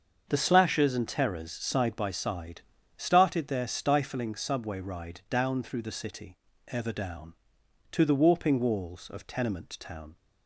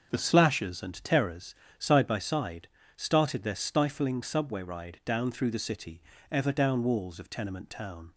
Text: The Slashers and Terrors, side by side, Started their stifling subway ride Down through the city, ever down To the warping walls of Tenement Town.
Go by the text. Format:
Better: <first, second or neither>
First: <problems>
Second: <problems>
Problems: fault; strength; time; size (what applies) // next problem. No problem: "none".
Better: first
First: starts louder than the rest; until 1.2 s; 6.5 dB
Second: starts louder than the rest; until 1.1 s; 6.5 dB // skips "To the warping"; at 6.8 s